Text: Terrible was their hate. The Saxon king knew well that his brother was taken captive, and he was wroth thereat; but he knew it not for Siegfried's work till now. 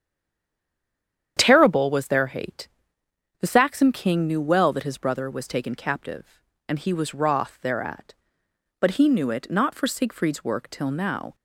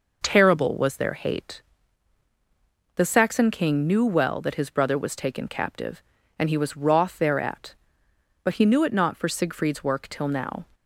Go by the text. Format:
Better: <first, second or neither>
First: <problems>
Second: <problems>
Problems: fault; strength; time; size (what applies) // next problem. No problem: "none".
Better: second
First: stays silent before the first word; noticeable; until 1.3 s; 1.3 s long // starts louder than the rest; strong; until 2.3 s; 9 dB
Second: none